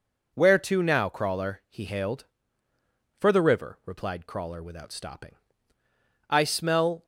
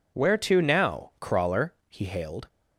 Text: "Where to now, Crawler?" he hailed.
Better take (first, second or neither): second